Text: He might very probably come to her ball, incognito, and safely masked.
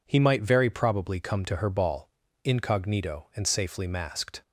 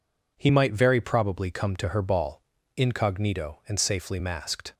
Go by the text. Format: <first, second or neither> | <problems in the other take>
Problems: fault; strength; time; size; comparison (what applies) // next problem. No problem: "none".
neither | none